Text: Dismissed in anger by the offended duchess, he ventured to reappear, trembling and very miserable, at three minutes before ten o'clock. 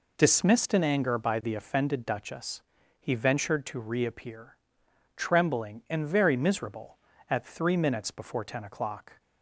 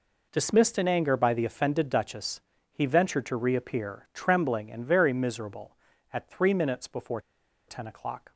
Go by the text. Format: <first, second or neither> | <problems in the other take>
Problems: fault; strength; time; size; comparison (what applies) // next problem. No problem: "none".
first | pauses between "before" and "ten"; noticeable; at 7.1 s; 0.48 s long